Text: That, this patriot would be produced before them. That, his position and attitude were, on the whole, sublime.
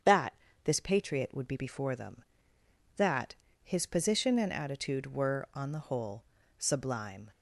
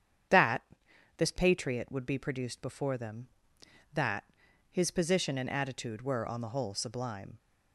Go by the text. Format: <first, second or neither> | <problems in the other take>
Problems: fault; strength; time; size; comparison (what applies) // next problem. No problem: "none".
second | starts louder than the rest; strong; until 1.3 s; 8 dB; strong in the second // skips "produced"; at 1.5 s